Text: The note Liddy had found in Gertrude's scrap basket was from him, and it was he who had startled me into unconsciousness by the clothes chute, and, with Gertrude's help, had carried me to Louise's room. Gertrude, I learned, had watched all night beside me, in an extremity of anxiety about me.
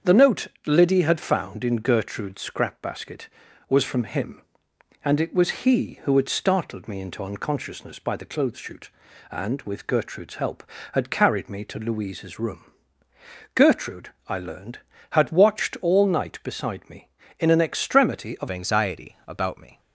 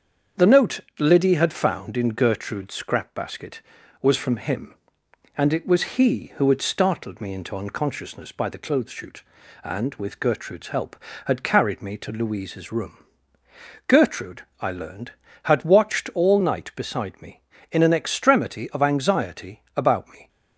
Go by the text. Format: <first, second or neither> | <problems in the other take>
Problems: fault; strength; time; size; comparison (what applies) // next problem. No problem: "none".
second | starts louder than the rest; strong; until 1.2 s; 7.5 dB; strong in the second // pauses between "note" and "Liddy"; slight; at 0.4 s; 0.18 s long; slight in the second // changes voice at "anxiety"; from 18.5 s on; 1.3 s long